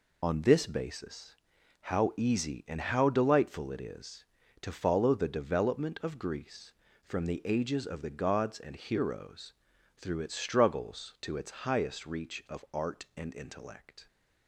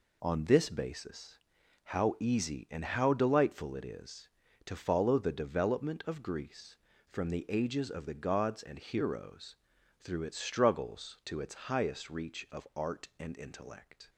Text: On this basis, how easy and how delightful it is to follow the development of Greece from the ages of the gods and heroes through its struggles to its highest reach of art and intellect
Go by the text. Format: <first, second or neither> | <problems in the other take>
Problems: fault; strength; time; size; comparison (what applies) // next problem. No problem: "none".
second | loses the start of "On"; at 0.2 s; 35 ms // pauses between "heroes" and "through"; noticeable; at 9.5 s; 0.46 s long; noticeable in the second